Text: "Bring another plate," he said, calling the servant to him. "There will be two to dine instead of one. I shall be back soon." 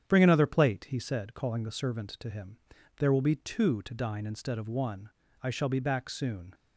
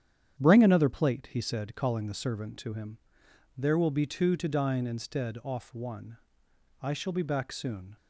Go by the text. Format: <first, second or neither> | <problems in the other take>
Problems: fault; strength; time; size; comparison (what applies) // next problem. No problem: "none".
first | starts louder than the rest; strong; until 1.4 s; 9 dB; strong in the first // says "off" for "of"; at 5.4 s